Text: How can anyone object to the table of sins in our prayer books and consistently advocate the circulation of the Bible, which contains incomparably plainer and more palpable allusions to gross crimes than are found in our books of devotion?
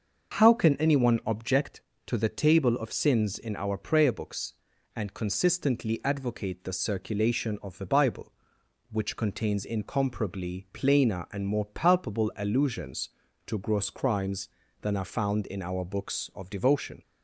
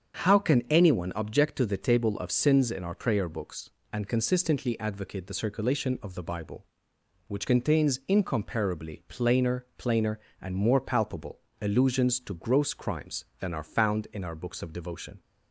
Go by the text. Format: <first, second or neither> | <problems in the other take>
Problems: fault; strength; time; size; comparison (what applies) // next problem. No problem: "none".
first | starts louder than the rest; until 1.3 s; 7 dB; noticeable in the first // says "plainer" twice; at 9.7 s // pauses between "palpable" and "allusions"; slight; at 11.3 s; 0.20 s long